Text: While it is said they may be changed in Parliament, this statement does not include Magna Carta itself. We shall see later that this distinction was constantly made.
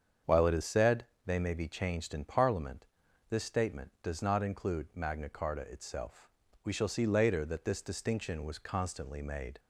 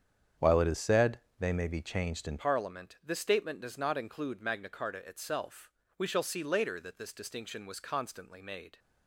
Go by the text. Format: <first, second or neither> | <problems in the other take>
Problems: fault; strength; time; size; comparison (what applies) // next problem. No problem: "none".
first | starts louder than the rest; strong; until 1.6 s; 8.5 dB; strong in the first // pauses between "said" and "they"; slight; at 1.1 s; 0.20 s long; slight in the first // changes voice at "Parliament"; from 2.3 s on; 6.4 s long